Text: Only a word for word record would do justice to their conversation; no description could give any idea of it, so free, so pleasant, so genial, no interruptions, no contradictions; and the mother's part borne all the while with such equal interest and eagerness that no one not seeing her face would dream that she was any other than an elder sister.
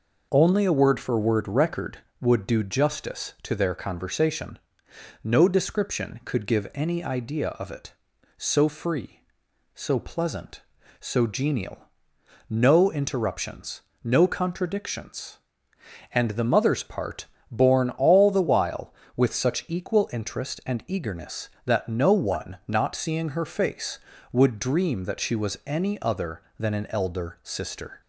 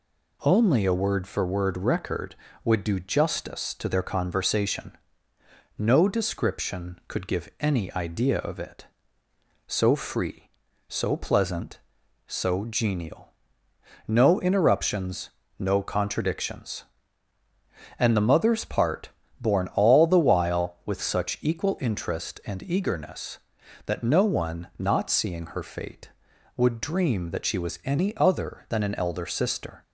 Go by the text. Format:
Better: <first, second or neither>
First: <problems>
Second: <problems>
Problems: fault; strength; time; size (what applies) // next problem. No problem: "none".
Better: first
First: pauses between "part" and "borne"; slight; at 17.2 s; 0.22 s long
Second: pauses between "part" and "borne"; slight; at 19.0 s; 0.32 s long // says "fate" for "face"; at 25.6 s